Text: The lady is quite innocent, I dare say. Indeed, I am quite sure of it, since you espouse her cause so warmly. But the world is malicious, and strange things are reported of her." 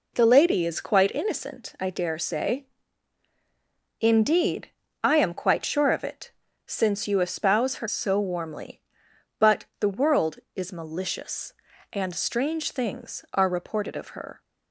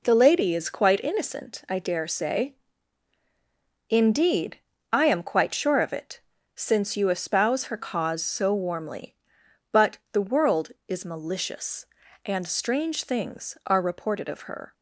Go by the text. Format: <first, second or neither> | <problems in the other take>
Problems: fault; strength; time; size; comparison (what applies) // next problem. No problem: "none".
second | skips "cause"; at 7.8 s